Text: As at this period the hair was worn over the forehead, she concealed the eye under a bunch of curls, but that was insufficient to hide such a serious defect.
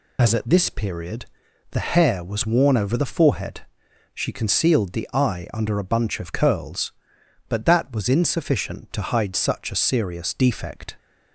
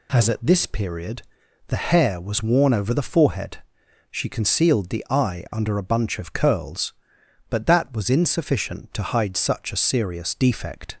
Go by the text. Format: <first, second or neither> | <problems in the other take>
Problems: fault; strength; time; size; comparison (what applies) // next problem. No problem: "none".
second | loses the start of "As"; at 0.1 s; 45 ms // pauses between "period" and "the"; noticeable; at 1.2 s; 0.46 s long; noticeable in the second